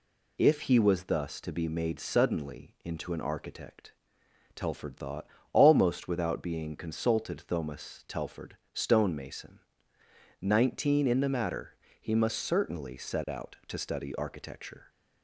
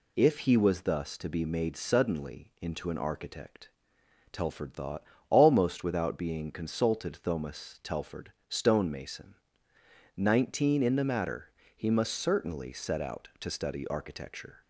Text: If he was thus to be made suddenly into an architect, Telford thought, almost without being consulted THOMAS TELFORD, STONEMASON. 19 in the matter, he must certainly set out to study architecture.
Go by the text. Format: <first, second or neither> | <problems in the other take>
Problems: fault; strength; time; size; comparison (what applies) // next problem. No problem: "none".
neither | none